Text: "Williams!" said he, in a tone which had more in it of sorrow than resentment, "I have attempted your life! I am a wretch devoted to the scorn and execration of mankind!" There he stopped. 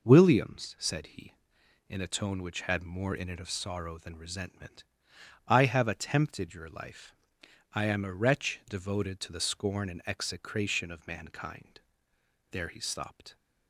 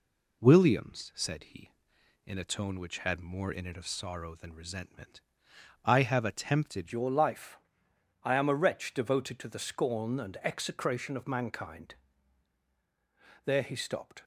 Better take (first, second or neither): first